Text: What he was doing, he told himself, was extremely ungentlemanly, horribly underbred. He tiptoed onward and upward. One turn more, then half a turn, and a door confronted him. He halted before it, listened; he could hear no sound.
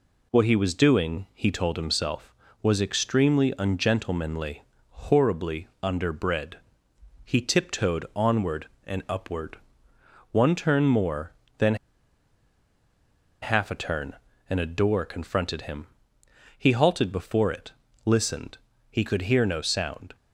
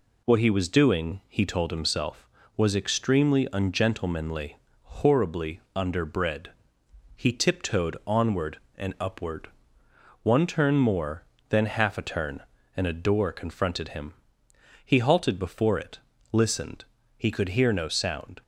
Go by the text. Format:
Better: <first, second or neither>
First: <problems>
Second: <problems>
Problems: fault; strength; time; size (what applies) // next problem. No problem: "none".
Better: second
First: pauses between "then" and "half"; strong; at 11.7 s; 1.6 s long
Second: none